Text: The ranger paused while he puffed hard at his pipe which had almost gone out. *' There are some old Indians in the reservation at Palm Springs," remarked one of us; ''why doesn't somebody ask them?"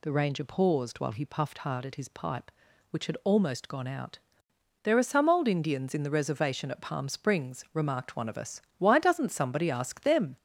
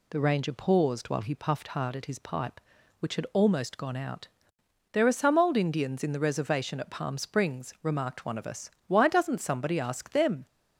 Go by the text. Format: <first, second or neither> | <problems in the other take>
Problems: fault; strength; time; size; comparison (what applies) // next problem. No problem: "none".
second | gets louder; noticeable; throughout; 4 dB